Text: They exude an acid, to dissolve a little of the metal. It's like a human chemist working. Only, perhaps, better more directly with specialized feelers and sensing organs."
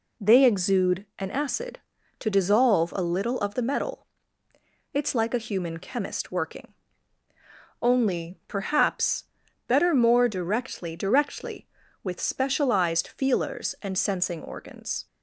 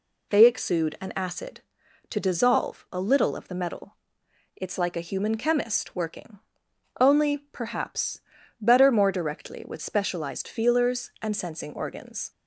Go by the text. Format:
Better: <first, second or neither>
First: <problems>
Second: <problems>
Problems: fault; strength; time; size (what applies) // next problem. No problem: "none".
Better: second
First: says "directly" twice; at 10.9 s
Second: none